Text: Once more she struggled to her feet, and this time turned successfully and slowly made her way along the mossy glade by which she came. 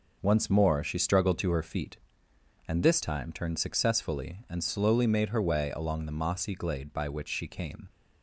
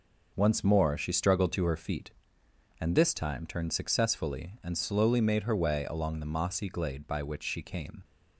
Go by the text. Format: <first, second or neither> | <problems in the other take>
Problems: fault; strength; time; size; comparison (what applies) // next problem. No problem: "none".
neither | none